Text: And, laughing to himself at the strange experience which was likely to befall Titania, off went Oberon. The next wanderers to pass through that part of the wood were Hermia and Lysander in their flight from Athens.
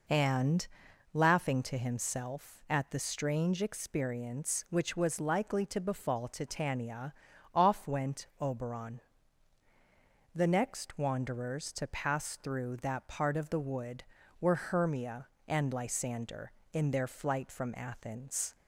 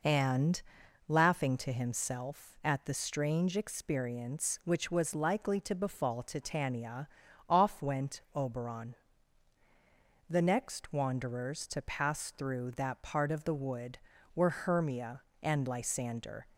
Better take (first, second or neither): first